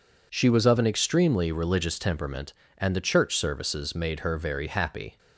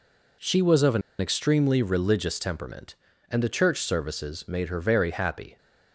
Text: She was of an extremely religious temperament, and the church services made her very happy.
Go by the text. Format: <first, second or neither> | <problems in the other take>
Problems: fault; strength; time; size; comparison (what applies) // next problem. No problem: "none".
first | pauses between "an" and "extremely"; slight; at 1.0 s; 0.19 s long